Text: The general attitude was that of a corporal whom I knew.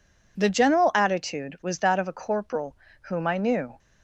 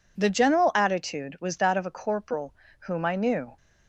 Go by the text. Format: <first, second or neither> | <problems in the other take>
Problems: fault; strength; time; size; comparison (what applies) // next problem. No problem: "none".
neither | pauses between "corporal" and "whom"; slight; the same in both